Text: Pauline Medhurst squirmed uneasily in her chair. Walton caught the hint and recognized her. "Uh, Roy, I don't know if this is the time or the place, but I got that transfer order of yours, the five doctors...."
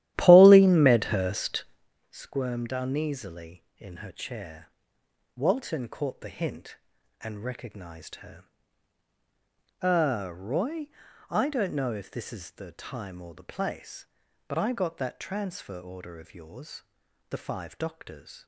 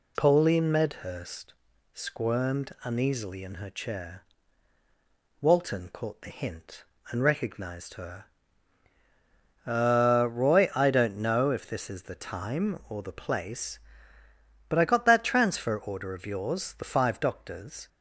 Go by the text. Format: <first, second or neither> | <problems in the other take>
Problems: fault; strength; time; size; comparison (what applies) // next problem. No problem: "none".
second | starts louder than the rest; strong; until 1.9 s; 13 dB // pauses between "Medhurst" and "squirmed"; at 1.6 s; 0.44 s long; also in the second